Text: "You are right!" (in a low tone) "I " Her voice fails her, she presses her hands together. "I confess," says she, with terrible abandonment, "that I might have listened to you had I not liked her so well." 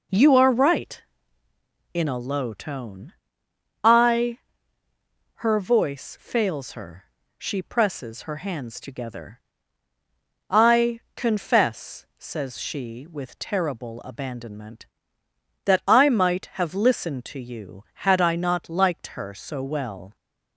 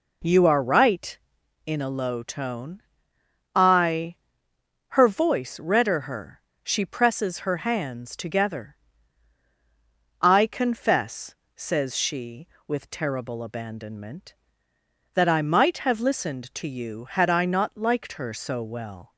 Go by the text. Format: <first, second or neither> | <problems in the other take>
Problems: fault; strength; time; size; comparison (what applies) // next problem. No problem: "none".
first | says "redder" for "fails"; at 5.5 s